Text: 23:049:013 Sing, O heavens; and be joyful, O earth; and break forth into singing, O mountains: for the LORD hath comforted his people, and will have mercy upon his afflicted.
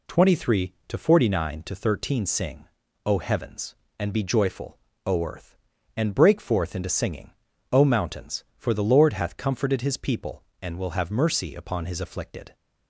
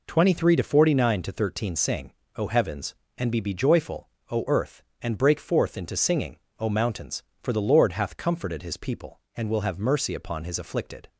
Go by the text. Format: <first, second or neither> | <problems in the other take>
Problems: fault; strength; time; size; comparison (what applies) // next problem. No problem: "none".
first | says "be" twice; at 3.4 s